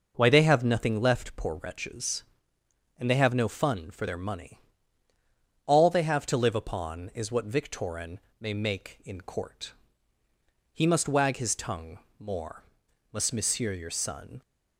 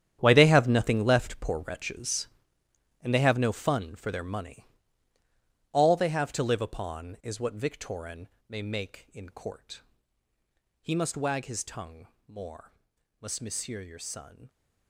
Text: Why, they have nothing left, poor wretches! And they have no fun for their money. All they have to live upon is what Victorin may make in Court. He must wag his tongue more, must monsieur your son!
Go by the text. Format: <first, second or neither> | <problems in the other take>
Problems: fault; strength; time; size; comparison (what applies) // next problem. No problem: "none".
first | gets quieter; strong; throughout; 13.5 dB // pauses between "Victorin" and "may"; slight; at 8.2 s; 0.20 s long; slight in the first // pauses between "tongue" and "more"; slight; at 12.0 s; 0.20 s long; slight in the first